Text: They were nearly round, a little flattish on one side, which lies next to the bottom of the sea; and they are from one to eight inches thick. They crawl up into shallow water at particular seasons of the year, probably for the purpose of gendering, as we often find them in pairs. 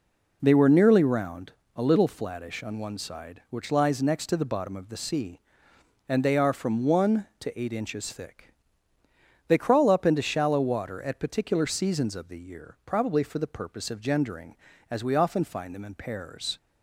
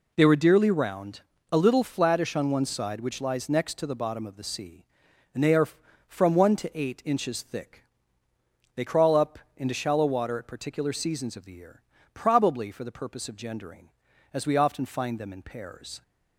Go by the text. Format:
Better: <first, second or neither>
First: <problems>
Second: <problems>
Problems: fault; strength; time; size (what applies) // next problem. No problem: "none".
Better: first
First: none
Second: says "dearly" for "nearly"; at 0.3 s // pauses between "up" and "into"; slight; at 9.3 s; 0.18 s long